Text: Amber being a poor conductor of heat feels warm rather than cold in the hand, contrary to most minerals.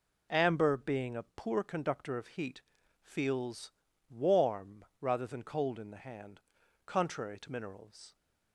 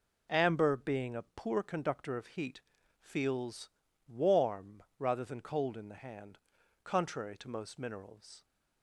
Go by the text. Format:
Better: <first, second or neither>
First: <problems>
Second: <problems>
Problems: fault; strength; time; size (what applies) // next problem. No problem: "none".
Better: second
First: pauses between "heat" and "feels"; at 2.6 s; 0.40 s long // pauses between "feels" and "warm"; at 3.7 s; 0.40 s long // pauses between "warm" and "rather"; slight; at 4.8 s; 0.16 s long // skips "most"; at 7.4 s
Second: pauses between "heat" and "feels"; at 2.5 s; 0.39 s long // pauses between "feels" and "warm"; at 3.6 s; 0.40 s long // pauses between "warm" and "rather"; slight; at 4.8 s; 0.16 s long